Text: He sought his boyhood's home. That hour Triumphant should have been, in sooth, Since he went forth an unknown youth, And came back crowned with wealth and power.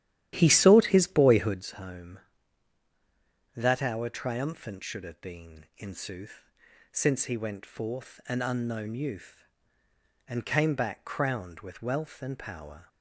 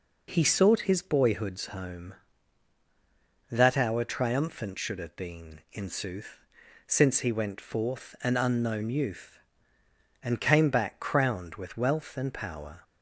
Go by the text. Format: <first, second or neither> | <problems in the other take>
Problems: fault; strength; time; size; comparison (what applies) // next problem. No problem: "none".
second | starts louder than the rest; strong; until 1.6 s; 12 dB